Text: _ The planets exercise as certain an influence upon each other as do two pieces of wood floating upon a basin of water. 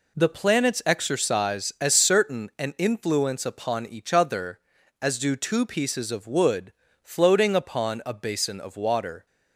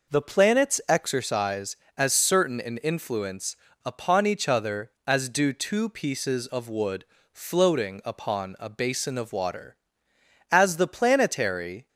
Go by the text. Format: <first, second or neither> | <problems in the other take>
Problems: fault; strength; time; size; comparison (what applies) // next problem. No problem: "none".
first | pauses between "influence" and "upon"; slight; at 3.5 s; 0.28 s long // pauses between "wood" and "floating"; slight; at 7.0 s; 0.30 s long; slight in the first // goes on to say "As the planetary"; from 10.4 s on; 1.3 s long